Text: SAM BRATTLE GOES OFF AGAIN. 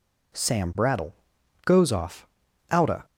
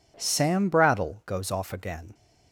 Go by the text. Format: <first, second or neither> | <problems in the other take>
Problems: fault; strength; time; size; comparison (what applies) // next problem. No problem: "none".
second | pauses between "BRATTLE" and "GOES"; noticeable; at 1.1 s; 0.50 s long // says "Outa" for "AGAIN"; at 2.6 s